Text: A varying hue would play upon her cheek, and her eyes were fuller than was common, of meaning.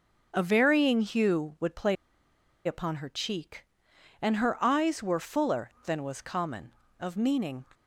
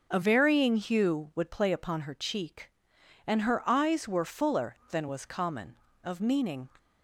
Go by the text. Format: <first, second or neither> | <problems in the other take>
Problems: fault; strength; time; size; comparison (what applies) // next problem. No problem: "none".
second | pauses between "play" and "upon"; noticeable; at 1.9 s; 0.70 s long